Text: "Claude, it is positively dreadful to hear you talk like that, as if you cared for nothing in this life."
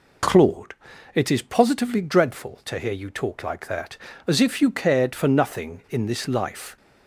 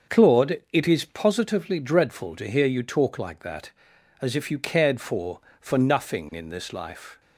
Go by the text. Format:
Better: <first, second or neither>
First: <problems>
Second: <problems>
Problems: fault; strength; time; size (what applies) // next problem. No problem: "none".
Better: first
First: none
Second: starts louder than the rest; until 1.2 s; 6 dB // says "for" twice; at 5.5 s